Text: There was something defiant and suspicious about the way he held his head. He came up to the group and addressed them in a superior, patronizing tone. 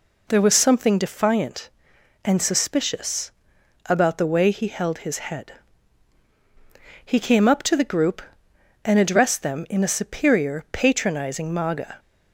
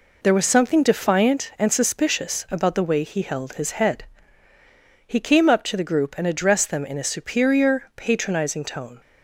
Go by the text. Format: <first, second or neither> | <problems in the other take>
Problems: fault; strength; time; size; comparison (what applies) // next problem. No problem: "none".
second | pauses between "suspicious" and "about"; noticeable; at 3.2 s; 0.56 s long // says "maga" for "tone"; at 11.5 s